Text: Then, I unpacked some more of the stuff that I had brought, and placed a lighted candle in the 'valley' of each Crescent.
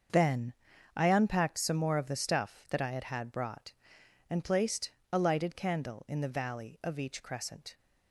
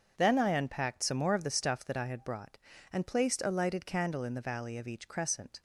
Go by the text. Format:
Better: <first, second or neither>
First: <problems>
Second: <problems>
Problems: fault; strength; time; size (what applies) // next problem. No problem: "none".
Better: second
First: starts louder than the rest; until 1.5 s; 6.5 dB // says "had" twice; at 3.0 s // pauses between "placed" and "a"; slight; at 4.9 s; 0.22 s long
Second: starts louder than the rest; until 1.1 s; 6.5 dB